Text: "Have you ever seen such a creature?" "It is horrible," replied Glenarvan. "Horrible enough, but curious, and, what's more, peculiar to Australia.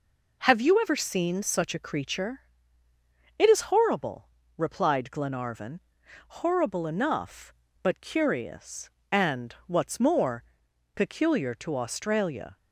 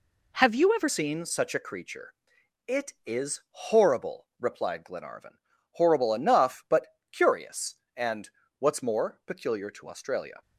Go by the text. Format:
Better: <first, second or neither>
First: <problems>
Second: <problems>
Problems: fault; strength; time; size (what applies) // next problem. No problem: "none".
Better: first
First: none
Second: changes voice at "seen"; from 0.8 s on; 9.6 s long // pauses between "but" and "curious"; slight; at 6.8 s; 0.24 s long